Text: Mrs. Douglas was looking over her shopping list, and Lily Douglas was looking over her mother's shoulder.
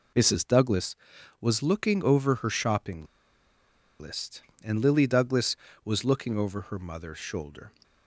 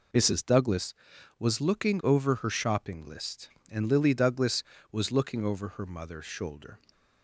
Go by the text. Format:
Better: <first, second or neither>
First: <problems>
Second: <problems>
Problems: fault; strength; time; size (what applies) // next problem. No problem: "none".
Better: second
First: pauses between "shopping" and "list"; noticeable; at 3.0 s; 0.93 s long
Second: none